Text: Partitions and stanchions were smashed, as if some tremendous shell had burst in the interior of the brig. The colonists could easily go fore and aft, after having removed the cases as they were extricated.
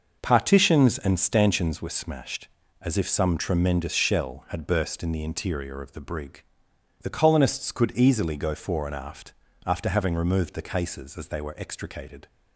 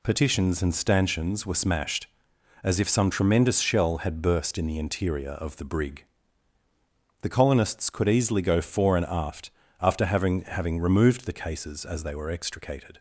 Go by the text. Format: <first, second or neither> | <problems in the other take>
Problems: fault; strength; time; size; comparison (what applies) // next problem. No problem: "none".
first | says "having" twice; at 10.4 s